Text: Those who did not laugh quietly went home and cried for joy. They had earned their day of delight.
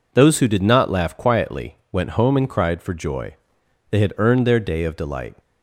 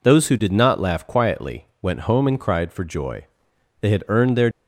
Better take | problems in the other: first | pauses between "quietly" and "went"; slight; at 1.6 s; 0.16 s long; slight in the first // stops before "day of delight"; at 4.5 s

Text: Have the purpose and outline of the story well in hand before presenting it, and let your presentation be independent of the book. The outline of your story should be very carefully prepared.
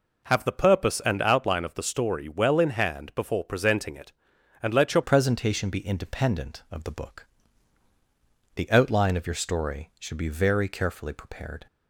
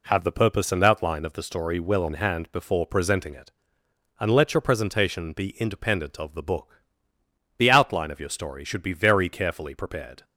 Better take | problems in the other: second | changes voice at "presentation"; from 5.0 s on; 6.6 s long

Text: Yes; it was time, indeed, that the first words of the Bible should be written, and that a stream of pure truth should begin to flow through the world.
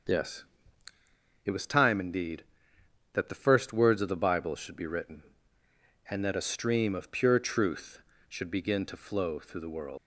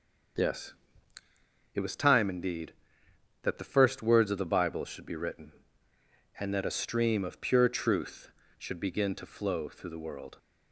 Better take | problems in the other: second | starts louder than the rest; noticeable; until 2.0 s; 6 dB; also in the second // leaves "world" unfinished; at 9.9 s; 105 ms

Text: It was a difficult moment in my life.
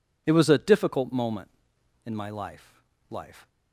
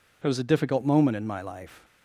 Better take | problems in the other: second | says "life" twice; at 3.1 s

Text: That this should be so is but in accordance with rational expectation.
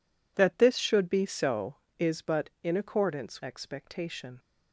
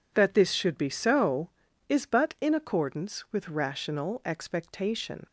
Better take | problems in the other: second | skips "with rational"; at 3.4 s

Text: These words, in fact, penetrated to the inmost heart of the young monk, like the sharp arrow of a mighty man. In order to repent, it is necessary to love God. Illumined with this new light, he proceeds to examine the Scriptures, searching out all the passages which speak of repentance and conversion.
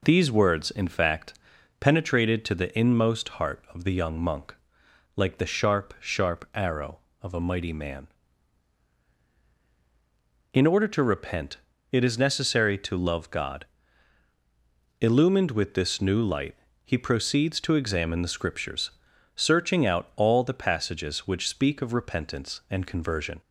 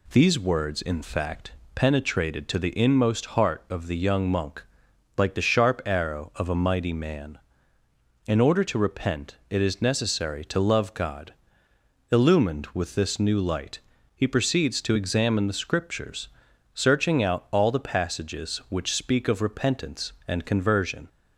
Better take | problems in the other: second | says "sharp" twice; at 5.9 s

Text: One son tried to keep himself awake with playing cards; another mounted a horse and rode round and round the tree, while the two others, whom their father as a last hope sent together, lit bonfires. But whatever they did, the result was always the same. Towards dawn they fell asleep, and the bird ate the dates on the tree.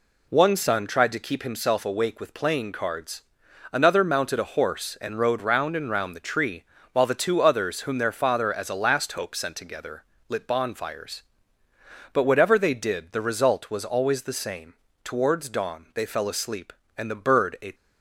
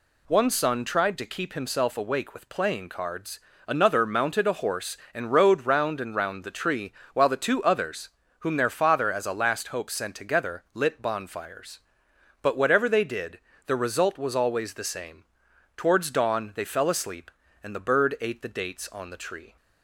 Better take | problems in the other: second | stops before "the dates on the tree"; at 17.7 s

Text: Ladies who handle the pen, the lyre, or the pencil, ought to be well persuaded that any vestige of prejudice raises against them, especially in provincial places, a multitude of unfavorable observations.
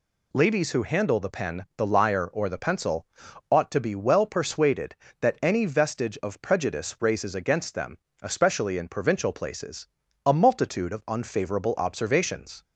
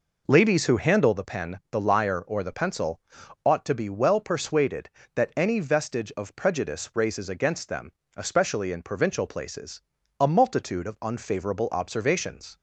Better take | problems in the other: first | starts louder than the rest; noticeable; until 1.2 s; 4.5 dB

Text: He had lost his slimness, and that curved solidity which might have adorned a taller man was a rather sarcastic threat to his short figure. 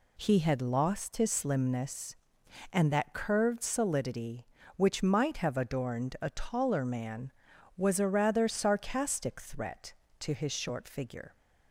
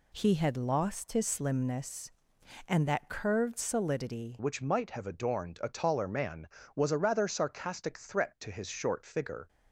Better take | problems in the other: first | changes voice at "which"; from 4.3 s on; 5.1 s long

